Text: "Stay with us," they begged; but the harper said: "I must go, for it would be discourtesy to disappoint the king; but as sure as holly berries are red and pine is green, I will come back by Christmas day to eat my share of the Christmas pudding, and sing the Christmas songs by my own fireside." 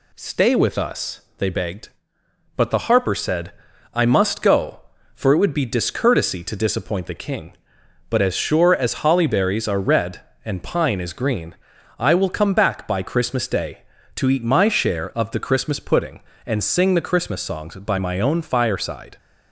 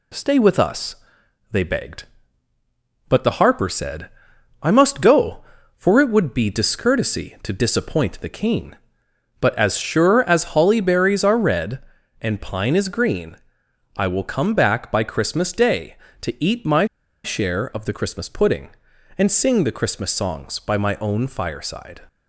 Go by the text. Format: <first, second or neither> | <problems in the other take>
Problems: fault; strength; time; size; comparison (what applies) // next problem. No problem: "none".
first | pauses between "my" and "share"; at 16.8 s; 0.39 s long